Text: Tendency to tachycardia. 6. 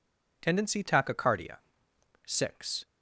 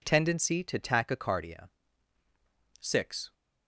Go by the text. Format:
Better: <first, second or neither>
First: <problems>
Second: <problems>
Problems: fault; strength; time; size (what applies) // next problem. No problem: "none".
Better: second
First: skips "to"; at 0.8 s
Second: none